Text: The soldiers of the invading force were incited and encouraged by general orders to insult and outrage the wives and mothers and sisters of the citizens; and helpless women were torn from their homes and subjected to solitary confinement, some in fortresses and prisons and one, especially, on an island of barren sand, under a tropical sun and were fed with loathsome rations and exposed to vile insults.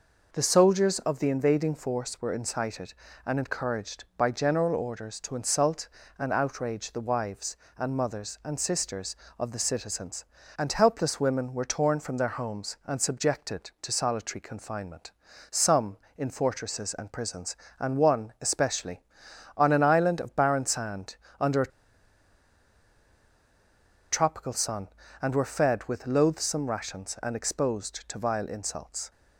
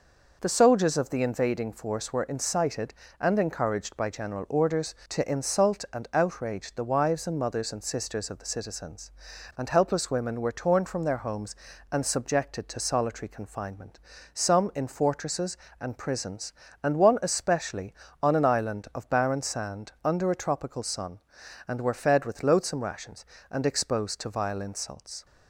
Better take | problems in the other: second | pauses between "a" and "tropical"; strong; at 21.7 s; 2.4 s long

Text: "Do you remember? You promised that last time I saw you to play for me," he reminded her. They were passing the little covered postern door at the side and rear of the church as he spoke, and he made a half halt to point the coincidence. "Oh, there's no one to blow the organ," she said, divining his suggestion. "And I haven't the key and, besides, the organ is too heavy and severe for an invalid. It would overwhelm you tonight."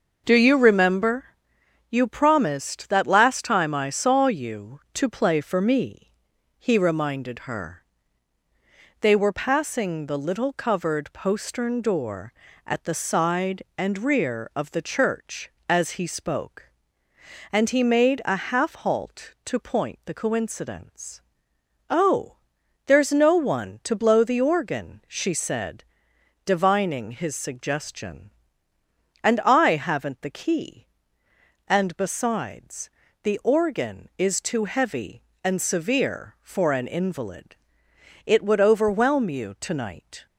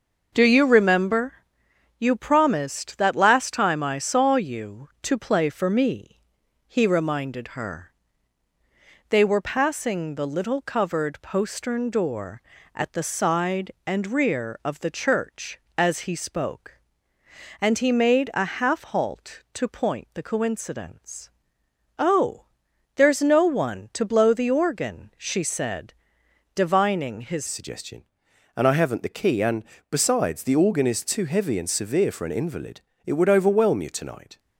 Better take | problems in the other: first | starts louder than the rest; until 1.3 s; 6.5 dB; also in the first // changes voice at "suggestion"; from 27.4 s on; 6.9 s long

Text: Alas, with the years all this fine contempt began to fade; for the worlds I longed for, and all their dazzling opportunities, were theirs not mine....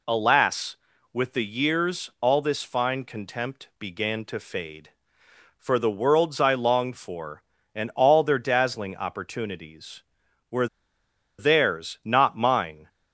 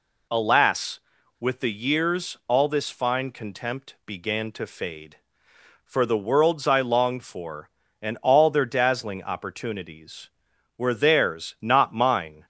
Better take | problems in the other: second | pauses between "were" and "theirs"; noticeable; at 10.6 s; 0.72 s long

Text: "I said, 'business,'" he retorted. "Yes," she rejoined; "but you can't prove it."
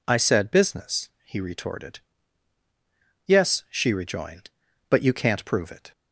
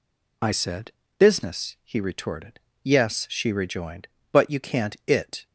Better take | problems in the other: first | skips "prove"; at 5.0 s

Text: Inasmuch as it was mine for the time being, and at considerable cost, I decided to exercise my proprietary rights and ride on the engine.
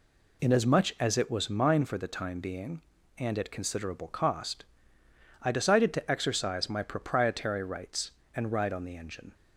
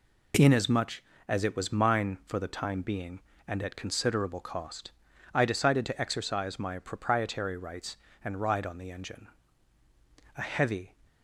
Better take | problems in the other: first | goes on to say "A heavy"; from 10.3 s on; 0.60 s long

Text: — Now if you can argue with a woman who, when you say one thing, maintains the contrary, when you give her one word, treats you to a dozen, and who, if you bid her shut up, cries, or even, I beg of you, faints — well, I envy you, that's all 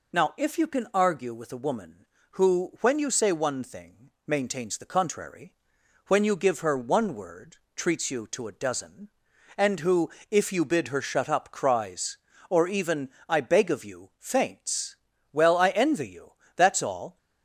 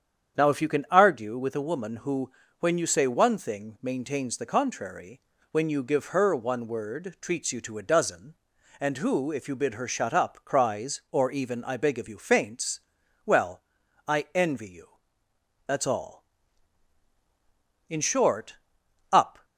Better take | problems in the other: first | starts louder than the rest; strong; until 1.4 s; 8.5 dB // goes on to say "In short up"; from 17.8 s on; 1.5 s long

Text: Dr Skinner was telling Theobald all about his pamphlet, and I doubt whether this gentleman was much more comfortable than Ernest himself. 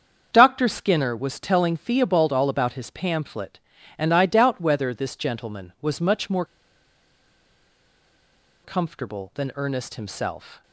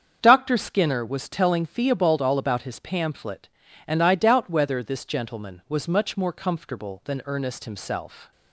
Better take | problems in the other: second | starts louder than the rest; strong; until 1.3 s; 7 dB; strong in the second // pauses between "more" and "comfortable"; strong; at 6.4 s; 2.1 s long

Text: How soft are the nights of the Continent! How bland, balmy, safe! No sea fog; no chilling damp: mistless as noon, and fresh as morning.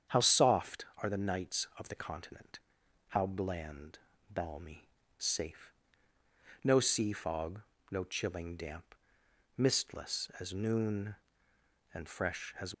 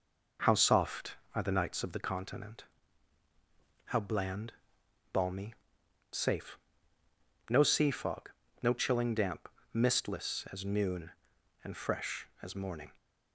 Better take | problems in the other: second | starts louder than the rest; strong; until 1.2 s; 8 dB // stops before "morning"; at 12.7 s

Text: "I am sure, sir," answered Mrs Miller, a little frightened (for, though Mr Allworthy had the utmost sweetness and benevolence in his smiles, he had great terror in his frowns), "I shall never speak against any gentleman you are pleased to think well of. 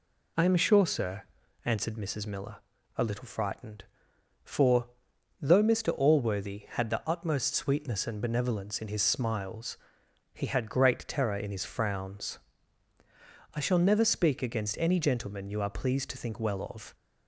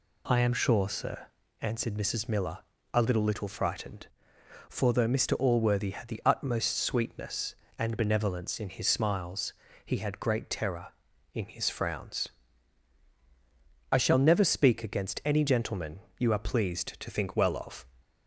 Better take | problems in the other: first | says "little" twice; at 3.2 s // pauses between "gentleman" and "you"; slight; at 16.0 s; 0.16 s long

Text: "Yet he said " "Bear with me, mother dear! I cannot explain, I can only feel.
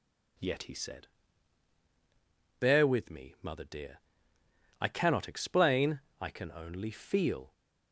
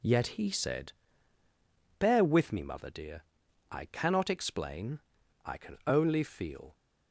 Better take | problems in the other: neither | none

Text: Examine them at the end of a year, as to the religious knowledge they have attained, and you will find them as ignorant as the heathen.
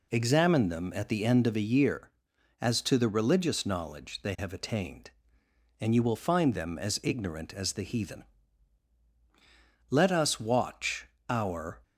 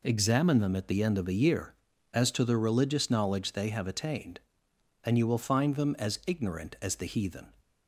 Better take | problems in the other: second | goes on to say "Let us watch our"; strong; from 9.8 s on; 1.9 s long

